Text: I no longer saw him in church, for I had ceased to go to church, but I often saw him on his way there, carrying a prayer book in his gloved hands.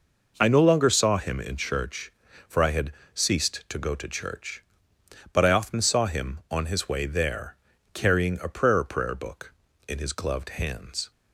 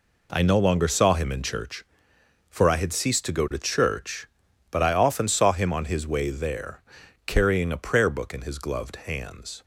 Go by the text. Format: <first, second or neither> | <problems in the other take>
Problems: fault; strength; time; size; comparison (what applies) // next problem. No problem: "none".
second | pauses between "had" and "ceased"; slight; at 2.9 s; 0.22 s long // says "prayer" twice; at 8.8 s